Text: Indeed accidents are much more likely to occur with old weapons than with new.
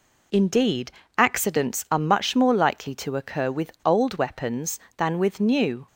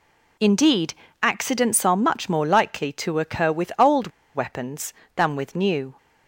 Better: first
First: pauses between "Indeed" and "accidents"; slight; at 0.9 s; 0.26 s long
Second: pauses between "Indeed" and "accidents"; slight; at 0.9 s; 0.28 s long // pauses between "old" and "weapons"; slight; at 4.0 s; 0.27 s long

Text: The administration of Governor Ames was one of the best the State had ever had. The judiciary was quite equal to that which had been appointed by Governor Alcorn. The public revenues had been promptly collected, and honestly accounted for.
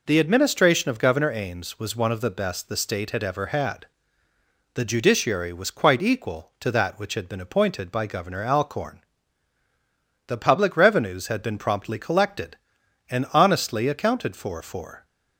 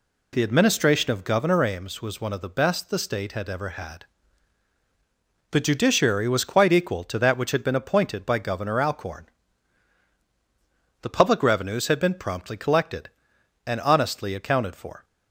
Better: second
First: says "for" twice; at 14.6 s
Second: none

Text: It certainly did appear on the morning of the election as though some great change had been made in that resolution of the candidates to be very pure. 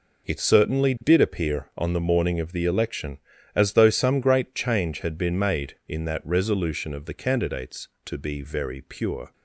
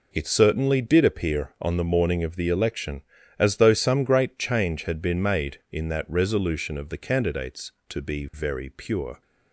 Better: neither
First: none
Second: none

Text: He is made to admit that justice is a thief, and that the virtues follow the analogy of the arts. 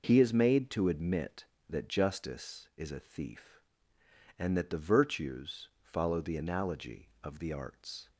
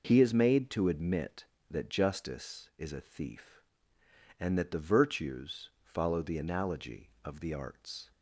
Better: neither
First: none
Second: none

